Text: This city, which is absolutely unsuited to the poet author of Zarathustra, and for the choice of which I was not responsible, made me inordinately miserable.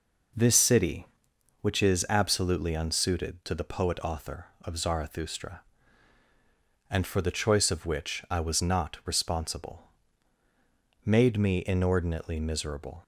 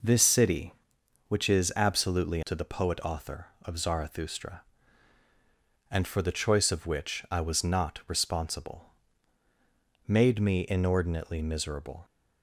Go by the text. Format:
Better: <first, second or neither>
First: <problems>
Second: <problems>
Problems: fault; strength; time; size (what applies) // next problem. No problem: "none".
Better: first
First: none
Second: skips "unsuited"; at 2.4 s